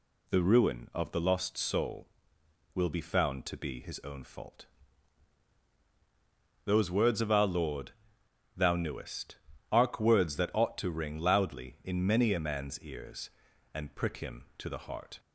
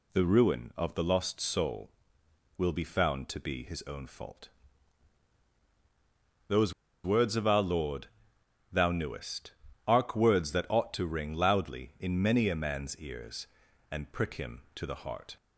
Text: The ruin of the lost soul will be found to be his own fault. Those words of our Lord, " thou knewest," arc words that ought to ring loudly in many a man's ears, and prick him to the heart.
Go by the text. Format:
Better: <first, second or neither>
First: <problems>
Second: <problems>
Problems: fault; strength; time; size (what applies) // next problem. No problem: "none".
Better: first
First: none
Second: pauses between "Those" and "words"; slight; at 6.7 s; 0.31 s long